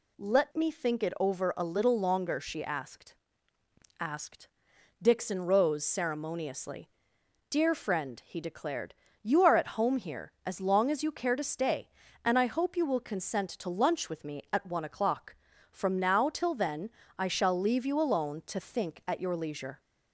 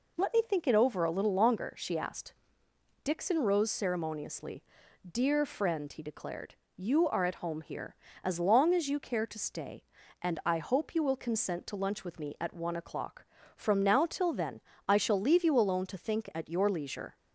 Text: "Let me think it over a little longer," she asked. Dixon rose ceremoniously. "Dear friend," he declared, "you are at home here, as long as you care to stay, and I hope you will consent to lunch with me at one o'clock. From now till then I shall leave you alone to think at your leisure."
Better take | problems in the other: second | says "asked" twice; at 3.9 s // pauses between "then" and "I"; slight; at 16.8 s; 0.28 s long; slight in the second

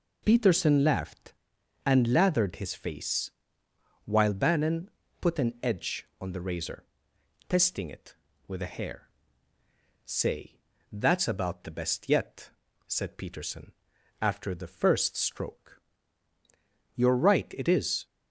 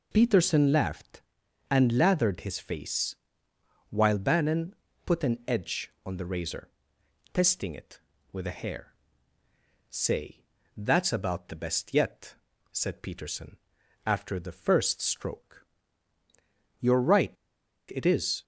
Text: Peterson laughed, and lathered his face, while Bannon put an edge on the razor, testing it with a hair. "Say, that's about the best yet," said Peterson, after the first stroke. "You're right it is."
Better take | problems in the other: first | pauses between "Bannon" and "put"; slight; at 4.7 s; 0.32 s long; slight in the first // pauses between "right" and "it"; noticeable; at 17.3 s; 0.57 s long

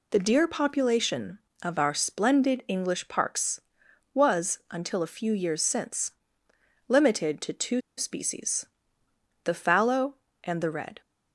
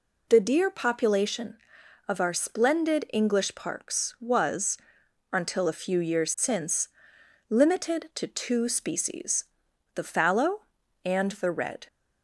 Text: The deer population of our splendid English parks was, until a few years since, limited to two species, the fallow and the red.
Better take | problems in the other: second | pauses between "two" and "species"; slight; at 7.7 s; 0.17 s long

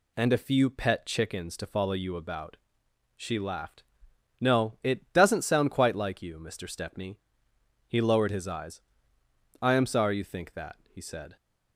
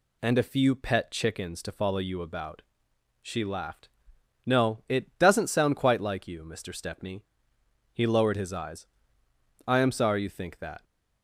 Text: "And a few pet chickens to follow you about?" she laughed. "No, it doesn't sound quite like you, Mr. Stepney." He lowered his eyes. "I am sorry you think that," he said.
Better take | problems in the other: first | stops before "he said"; at 10.8 s

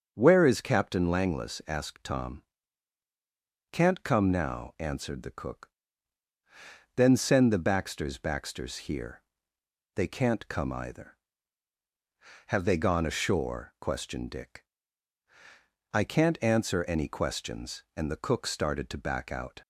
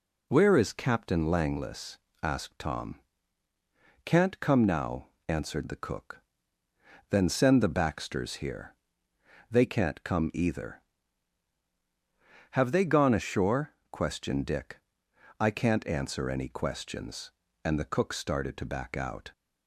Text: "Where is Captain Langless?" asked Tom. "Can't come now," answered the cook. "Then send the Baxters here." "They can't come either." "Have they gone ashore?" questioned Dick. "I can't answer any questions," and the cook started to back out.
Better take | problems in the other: second | starts louder than the rest; until 1.2 s; 6.5 dB // says "Baxters" twice; at 8.1 s

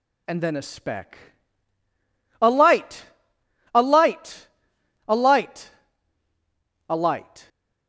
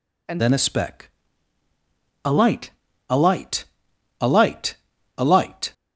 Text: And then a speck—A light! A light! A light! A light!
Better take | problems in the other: first | changes voice at "then"; from 0.3 s on; 5.4 s long

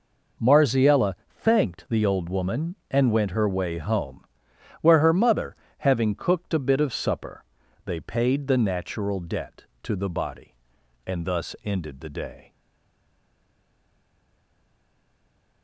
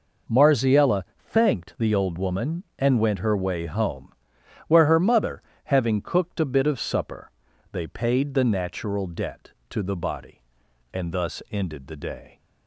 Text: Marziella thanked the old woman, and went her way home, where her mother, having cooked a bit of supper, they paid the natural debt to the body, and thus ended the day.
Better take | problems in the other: second | pauses between "Marziella" and "thanked"; slight; at 1.1 s; 0.16 s long; slight in the second // stays silent after the last word; strong; from 12.5 s on; 3.1 s long

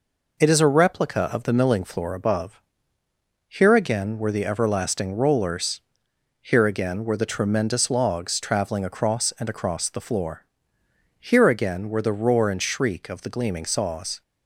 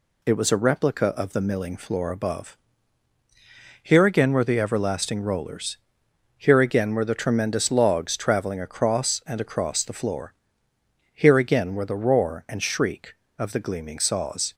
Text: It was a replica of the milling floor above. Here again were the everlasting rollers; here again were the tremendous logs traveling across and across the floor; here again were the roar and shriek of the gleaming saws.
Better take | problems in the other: second | says "is" for "was"; at 0.4 s

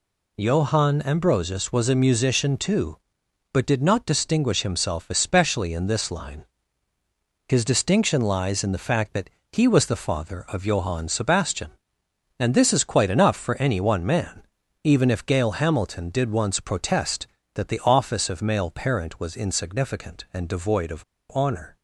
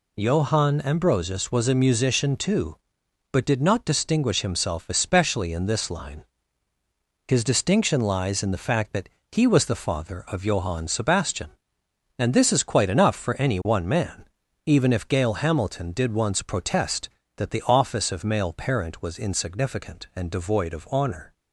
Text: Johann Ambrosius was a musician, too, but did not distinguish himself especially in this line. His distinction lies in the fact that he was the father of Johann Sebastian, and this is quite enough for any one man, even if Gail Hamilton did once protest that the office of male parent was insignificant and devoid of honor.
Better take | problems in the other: second | pauses between "that" and "he"; slight; at 9.2 s; 0.22 s long; slight in the second // pauses between "of" and "honor"; slight; at 21.0 s; 0.30 s long

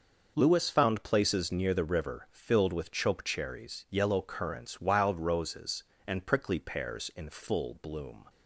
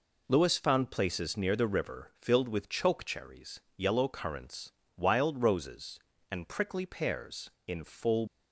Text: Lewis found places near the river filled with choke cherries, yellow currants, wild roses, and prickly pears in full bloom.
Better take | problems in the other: first | stops before "bloom"; at 8.2 s

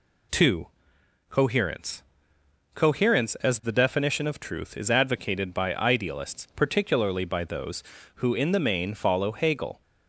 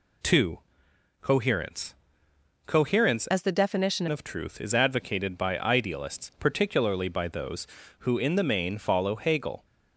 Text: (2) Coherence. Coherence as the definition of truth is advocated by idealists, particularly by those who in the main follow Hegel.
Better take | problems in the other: first | changes voice from "as" to "definition"; from 3.2 to 4.0 s; 0.8 s long

